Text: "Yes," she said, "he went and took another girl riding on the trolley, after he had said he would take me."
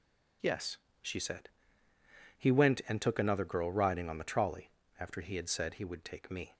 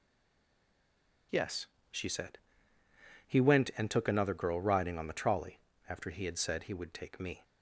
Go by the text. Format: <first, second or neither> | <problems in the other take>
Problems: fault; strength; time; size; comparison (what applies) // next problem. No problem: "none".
first | stays silent before the first word; noticeable; until 1.3 s; 1.3 s long